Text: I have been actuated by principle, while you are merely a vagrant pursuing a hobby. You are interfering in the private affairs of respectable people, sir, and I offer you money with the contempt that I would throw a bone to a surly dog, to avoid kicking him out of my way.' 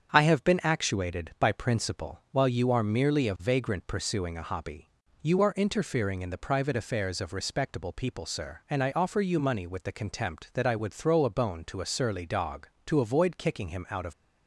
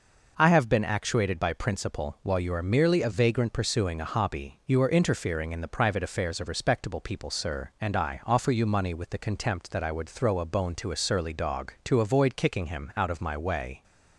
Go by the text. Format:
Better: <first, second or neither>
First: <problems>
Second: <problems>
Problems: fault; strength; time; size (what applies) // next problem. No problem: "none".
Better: second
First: starts louder than the rest; strong; until 1.1 s; 7.5 dB // stops before "my way"; at 14.1 s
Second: none